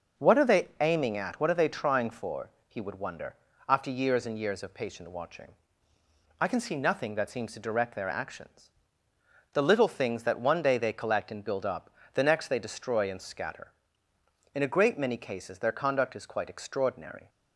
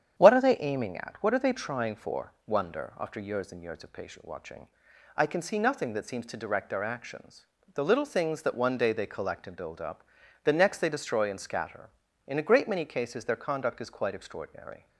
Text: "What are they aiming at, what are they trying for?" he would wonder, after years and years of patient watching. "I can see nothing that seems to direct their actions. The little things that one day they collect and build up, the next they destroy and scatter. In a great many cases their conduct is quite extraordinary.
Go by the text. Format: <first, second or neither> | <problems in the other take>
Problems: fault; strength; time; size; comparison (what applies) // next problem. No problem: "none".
first | starts louder than the rest; strong; until 1.2 s; 9 dB // skips "he would"; at 2.3 s